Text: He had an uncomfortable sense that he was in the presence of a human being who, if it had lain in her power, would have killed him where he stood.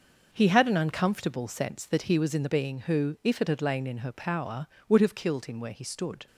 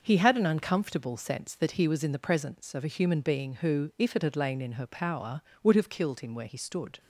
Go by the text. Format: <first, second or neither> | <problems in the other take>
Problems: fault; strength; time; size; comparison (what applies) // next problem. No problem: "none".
second | starts louder than the rest; until 1.3 s; 6.5 dB; noticeable in the second // skips "presence of a human"; at 2.4 s